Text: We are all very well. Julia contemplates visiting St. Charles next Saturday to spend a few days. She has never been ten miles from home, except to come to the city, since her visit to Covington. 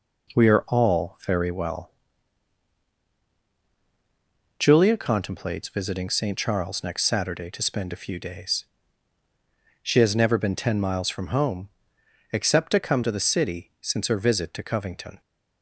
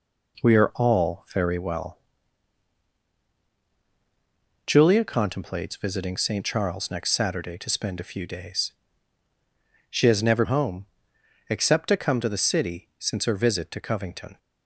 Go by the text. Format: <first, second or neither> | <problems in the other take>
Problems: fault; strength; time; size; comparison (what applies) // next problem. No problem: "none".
first | skips "been ten miles from"; at 10.4 s